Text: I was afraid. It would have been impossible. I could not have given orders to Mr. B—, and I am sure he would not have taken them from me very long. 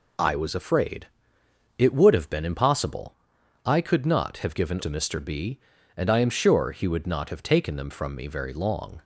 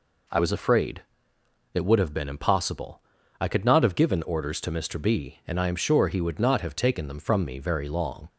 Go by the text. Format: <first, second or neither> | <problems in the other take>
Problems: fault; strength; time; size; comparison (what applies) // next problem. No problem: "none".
second | skips "orders"; at 4.7 s